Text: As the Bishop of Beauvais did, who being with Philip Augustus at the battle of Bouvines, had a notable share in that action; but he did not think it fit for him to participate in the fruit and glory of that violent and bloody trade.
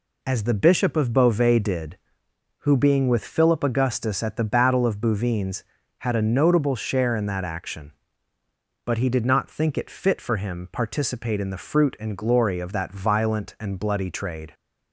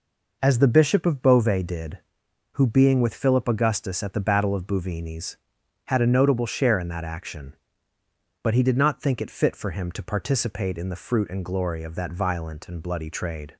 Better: second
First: skips "to"; at 10.6 s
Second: none

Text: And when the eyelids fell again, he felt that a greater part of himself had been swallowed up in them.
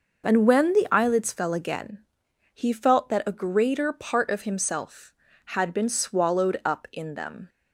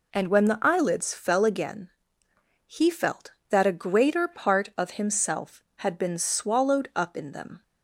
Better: neither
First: none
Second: none

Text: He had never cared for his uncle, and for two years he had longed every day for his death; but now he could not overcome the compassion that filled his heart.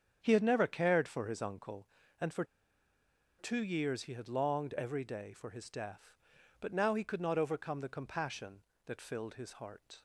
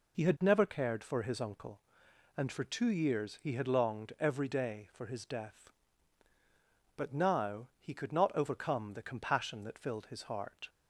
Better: second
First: starts louder than the rest; strong; until 1.2 s; 8 dB // pauses between "for" and "two"; noticeable; at 2.4 s; 0.95 s long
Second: none

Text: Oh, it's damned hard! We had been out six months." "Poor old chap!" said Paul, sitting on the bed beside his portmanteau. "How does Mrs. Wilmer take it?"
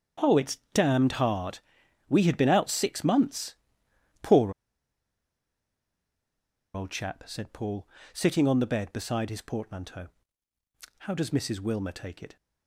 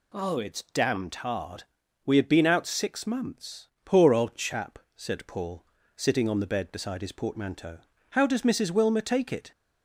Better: second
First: starts louder than the rest; strong; until 1.3 s; 8 dB // pauses between "it's" and "damned"; slight; at 0.5 s; 0.16 s long // pauses between "Poor" and "old"; strong; at 4.5 s; 2.2 s long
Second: none

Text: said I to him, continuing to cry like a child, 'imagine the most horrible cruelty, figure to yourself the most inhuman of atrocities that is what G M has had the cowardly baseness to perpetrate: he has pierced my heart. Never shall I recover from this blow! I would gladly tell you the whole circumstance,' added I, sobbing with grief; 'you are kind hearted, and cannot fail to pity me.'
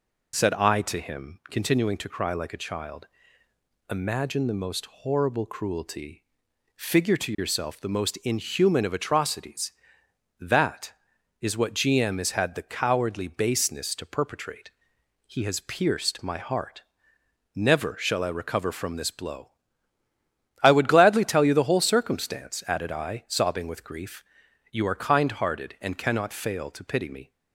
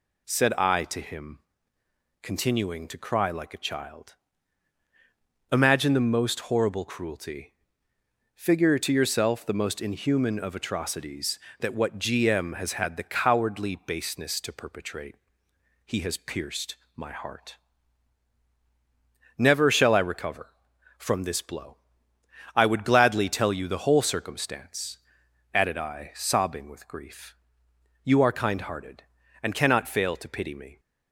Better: first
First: none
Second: skips "is"; at 11.7 s // pauses between "pierced" and "my"; slight; at 16.7 s; 0.20 s long

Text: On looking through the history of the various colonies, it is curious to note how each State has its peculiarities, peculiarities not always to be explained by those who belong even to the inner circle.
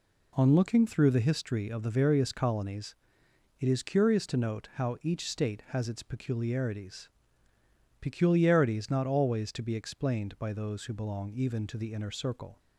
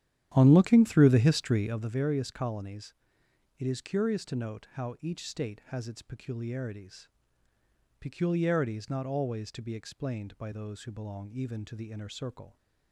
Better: first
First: none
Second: starts louder than the rest; strong; until 1.9 s; 11 dB

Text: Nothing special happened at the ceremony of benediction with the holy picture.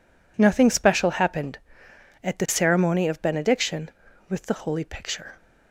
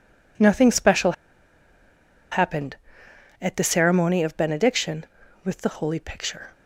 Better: first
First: none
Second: pauses between "special" and "happened"; at 1.1 s; 1.1 s long

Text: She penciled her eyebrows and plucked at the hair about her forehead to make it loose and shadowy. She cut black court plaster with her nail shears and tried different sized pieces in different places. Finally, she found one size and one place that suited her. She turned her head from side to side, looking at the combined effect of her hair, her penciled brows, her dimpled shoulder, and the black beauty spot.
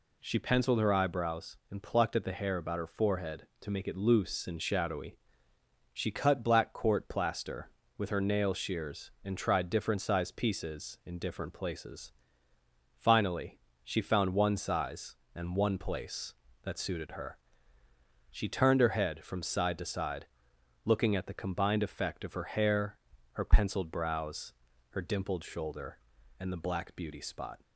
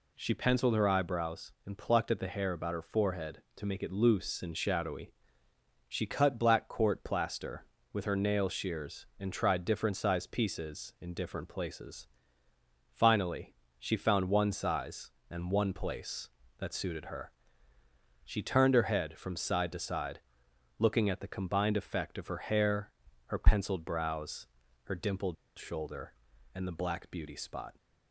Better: first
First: none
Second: pauses between "dimpled" and "shoulder"; slight; at 25.3 s; 0.23 s long

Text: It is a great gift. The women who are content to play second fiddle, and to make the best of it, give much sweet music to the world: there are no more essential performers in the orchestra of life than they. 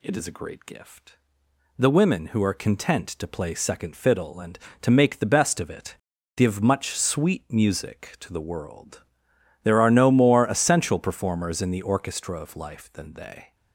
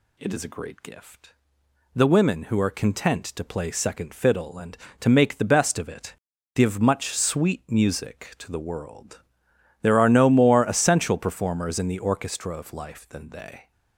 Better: neither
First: none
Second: none

